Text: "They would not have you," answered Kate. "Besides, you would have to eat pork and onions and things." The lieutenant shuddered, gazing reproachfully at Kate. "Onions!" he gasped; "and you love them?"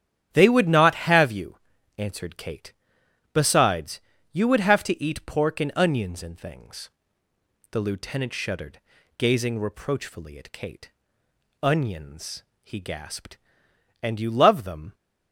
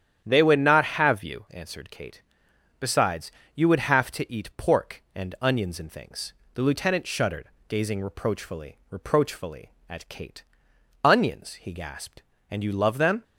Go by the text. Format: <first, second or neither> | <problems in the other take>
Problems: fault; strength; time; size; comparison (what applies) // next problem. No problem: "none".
first | starts louder than the rest; strong; until 1.2 s; 9.5 dB; strong in the first // says "reproachfully" twice; at 8.8 s